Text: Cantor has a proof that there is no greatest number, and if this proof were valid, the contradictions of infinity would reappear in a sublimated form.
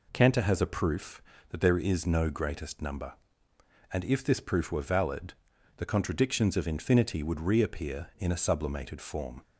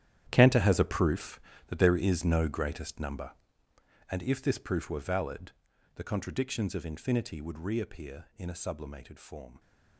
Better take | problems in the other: first | gets quieter; strong; throughout; 14.5 dB

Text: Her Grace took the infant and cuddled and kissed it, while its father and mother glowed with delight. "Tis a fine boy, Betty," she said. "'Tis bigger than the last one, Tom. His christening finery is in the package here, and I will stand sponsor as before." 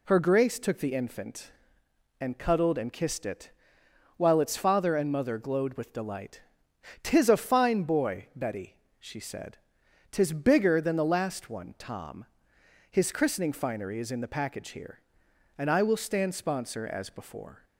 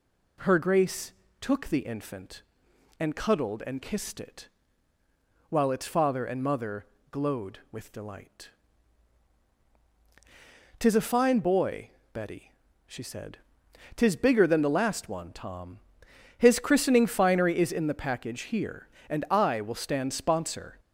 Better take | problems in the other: first | pauses between "Grace" and "took"; slight; at 1.1 s; 0.30 s long // pauses between "mother" and "glowed"; slight; at 6.8 s; 0.26 s long // stops before "as before"; at 20.7 s

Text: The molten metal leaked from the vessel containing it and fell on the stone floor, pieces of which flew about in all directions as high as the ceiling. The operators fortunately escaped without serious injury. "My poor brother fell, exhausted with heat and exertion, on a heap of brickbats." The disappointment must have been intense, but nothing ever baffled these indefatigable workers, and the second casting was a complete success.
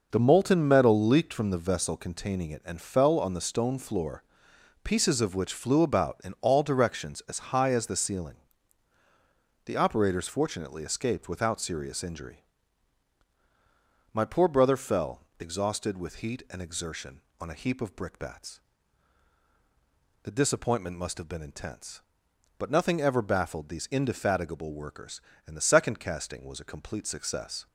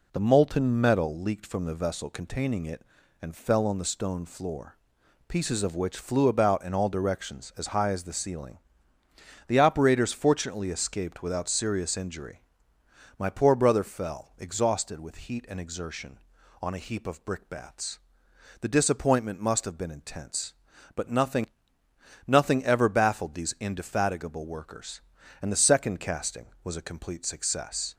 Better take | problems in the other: first | says "nothing" twice; at 22.2 s

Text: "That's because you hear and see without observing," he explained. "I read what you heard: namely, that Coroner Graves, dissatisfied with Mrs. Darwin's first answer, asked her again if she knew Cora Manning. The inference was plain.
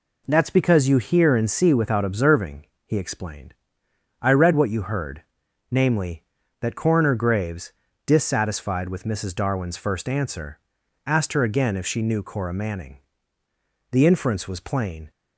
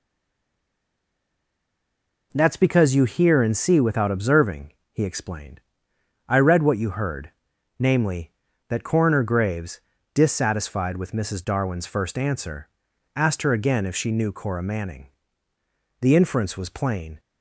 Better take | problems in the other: first | stays silent before the first word; until 2.3 s; 2.3 s long

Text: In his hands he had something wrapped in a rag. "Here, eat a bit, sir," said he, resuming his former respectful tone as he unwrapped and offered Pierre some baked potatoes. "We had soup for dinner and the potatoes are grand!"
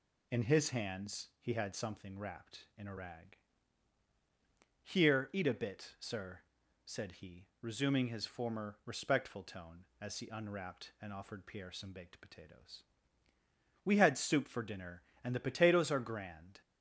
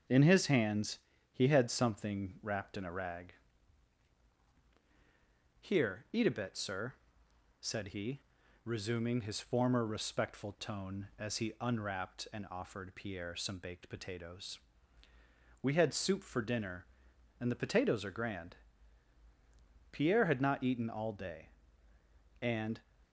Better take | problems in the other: first | starts louder than the rest; until 1.4 s; 6.5 dB // pauses between "hands" and "he"; slight; at 0.9 s; 0.34 s long // goes on to say "Pierre had not eaten all day and"; strong; from 19.9 s on; 2.8 s long

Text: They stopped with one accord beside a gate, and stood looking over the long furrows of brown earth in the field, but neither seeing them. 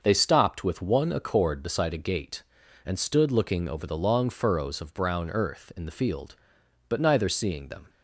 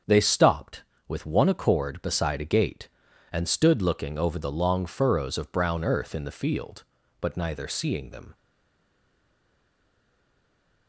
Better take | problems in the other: first | starts louder than the rest; until 1.3 s; 7 dB; also in the first // stays silent after the last word; strong; from 8.3 s on; 2.5 s long

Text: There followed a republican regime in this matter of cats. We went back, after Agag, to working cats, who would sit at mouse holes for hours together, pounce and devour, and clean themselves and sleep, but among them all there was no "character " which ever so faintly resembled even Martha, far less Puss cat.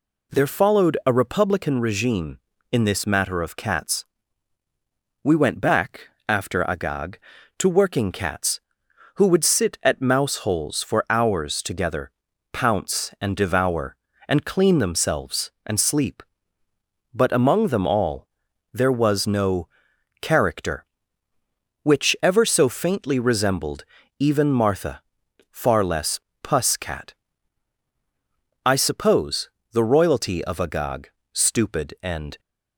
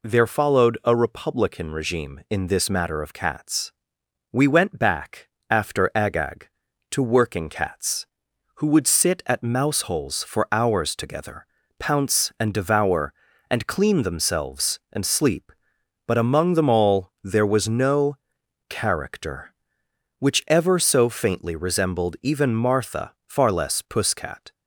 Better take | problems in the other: second | pauses between "all" and "there"; at 18.2 s; 0.44 s long // pauses between "no" and "character"; noticeable; at 19.6 s; 0.54 s long; noticeable in the second // pauses between "resembled" and "even"; slight; at 23.8 s; 0.36 s long // pauses between "less" and "Puss"; slight; at 26.1 s; 0.24 s long // goes on to say "I suppose the royalty of Agag stupid and"; strong; from 28.6 s on; 3.7 s long

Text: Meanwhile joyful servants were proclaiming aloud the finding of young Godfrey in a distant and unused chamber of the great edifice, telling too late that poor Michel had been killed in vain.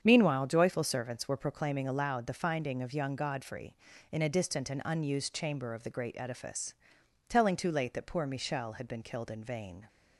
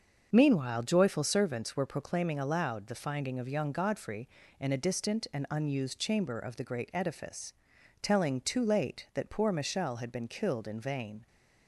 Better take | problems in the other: neither | starts louder than the rest; the same in both

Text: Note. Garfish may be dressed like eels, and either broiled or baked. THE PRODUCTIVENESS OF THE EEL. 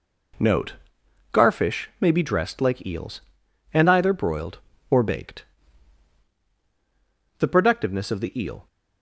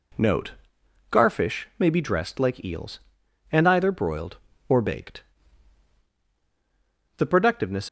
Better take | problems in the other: first | stops before "OF THE EEL"; at 7.8 s

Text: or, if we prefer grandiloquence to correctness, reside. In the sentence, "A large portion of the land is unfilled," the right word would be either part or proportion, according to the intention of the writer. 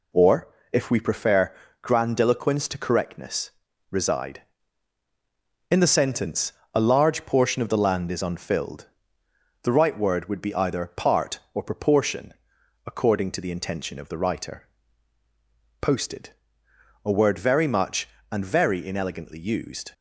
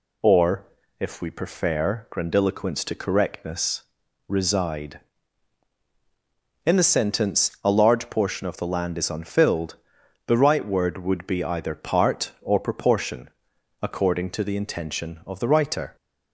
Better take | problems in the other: second | pauses between "prefer" and "grandiloquence"; slight; at 1.5 s; 0.28 s long // goes on to say "POSTED A word very much and very inelegantly used"; strong; from 15.8 s on; 4.1 s long

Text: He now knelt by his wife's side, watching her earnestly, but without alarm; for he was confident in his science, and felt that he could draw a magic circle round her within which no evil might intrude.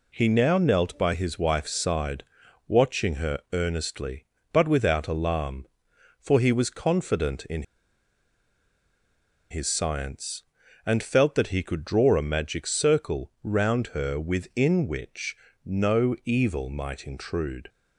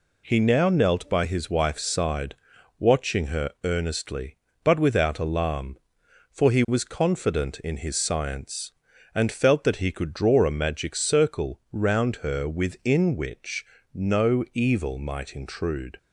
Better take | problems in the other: second | pauses between "in" and "his"; strong; at 7.6 s; 1.8 s long // pauses between "which" and "no"; slight; at 15.3 s; 0.30 s long; slight in the second

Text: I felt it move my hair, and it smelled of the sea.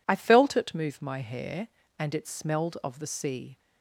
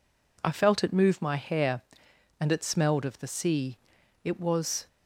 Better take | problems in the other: first | goes on to say "It was"; noticeable; from 4.2 s on; 0.64 s long

